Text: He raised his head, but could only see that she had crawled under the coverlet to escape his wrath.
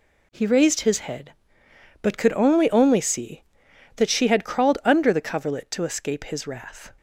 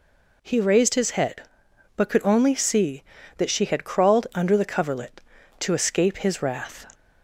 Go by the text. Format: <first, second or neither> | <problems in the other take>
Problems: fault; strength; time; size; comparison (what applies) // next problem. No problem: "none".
second | says "only" twice; at 2.6 s